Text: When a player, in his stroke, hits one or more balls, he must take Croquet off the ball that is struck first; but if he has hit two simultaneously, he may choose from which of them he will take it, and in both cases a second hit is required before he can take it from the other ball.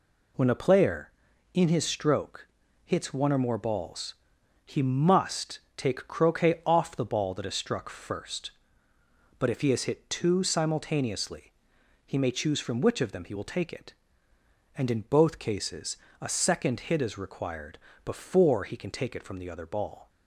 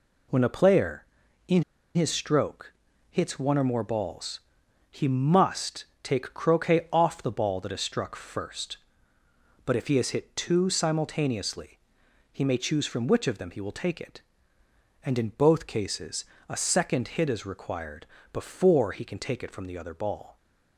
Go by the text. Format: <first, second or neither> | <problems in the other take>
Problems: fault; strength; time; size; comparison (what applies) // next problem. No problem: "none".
first | pauses between "in" and "his"; slight; at 1.6 s; 0.31 s long // pauses between "must" and "take"; slight; at 5.8 s; 0.18 s long; slight in the first // pauses between "cases" and "a"; slight; at 16.2 s; 0.22 s long; slight in the first // pauses between "required" and "before"; slight; at 18.0 s; 0.26 s long; slight in the first